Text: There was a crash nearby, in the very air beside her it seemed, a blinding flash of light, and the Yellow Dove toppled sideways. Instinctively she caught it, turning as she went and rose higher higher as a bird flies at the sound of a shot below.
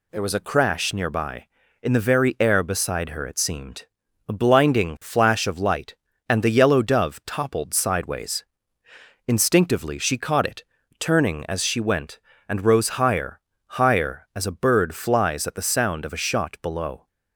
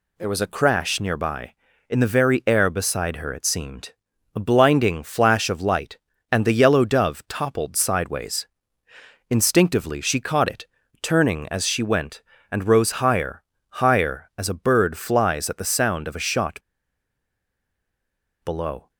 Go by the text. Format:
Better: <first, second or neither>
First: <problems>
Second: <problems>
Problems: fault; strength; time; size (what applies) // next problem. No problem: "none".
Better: first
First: pauses between "higher" and "higher"; at 13.3 s; 0.38 s long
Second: pauses between "higher" and "higher"; at 13.4 s; 0.38 s long // pauses between "shot" and "below"; strong; at 16.5 s; 1.8 s long